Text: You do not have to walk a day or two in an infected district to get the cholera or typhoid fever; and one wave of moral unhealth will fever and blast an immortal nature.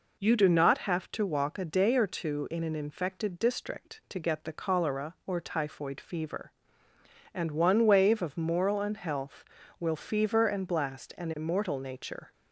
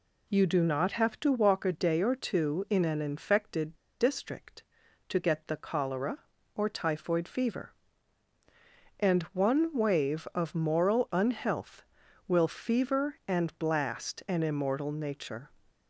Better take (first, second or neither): first